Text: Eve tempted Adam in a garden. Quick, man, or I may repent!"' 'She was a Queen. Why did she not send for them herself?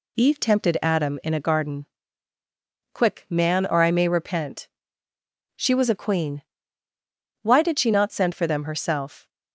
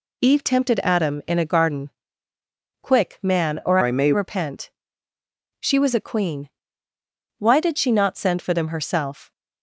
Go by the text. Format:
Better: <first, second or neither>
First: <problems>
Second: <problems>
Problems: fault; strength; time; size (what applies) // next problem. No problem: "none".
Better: first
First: none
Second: changes voice from "I" to "may"; from 3.8 to 4.1 s; 0.3 s long